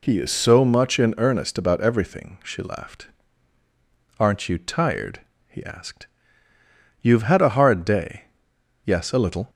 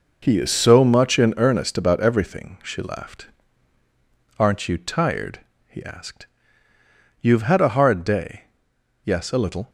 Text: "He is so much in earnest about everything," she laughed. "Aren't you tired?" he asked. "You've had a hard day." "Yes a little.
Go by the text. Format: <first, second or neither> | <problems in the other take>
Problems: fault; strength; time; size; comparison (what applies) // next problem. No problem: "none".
first | gets quieter; strong; throughout; 9.5 dB